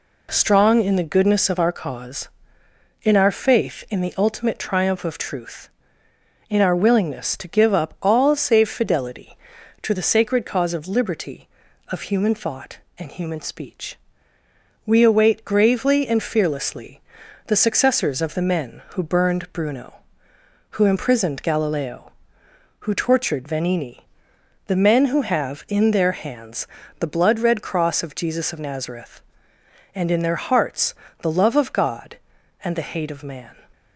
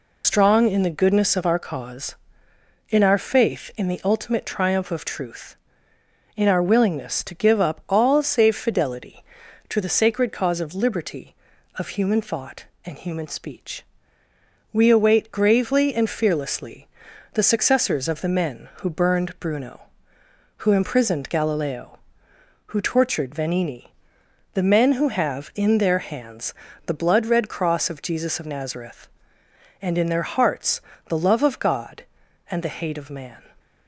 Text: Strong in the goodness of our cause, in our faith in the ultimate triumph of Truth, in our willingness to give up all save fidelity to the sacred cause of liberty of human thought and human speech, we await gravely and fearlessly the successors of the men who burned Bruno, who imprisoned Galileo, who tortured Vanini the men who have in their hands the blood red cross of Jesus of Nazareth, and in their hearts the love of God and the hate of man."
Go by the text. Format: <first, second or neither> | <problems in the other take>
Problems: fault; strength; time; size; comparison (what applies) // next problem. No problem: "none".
first | loses the start of "Strong"; at 0.2 s; 95 ms // pauses between "fearlessly" and "the"; noticeable; at 16.8 s; 0.46 s long; noticeable in the first // pauses between "Vanini" and "the"; noticeable; at 23.9 s; 0.62 s long; noticeable in the first // pauses between "hands" and "the"; slight; at 26.5 s; 0.32 s long; slight in the first // pauses between "hearts" and "the"; slight; at 30.8 s; 0.28 s long; slight in the first